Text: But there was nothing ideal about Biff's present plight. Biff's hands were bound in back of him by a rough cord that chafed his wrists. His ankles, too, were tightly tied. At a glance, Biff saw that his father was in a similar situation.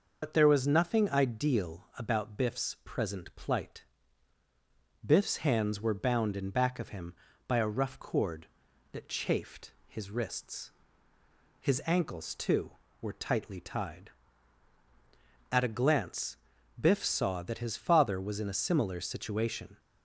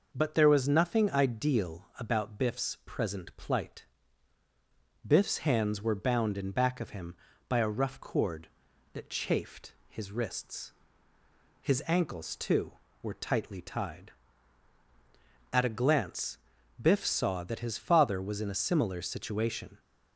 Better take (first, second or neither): second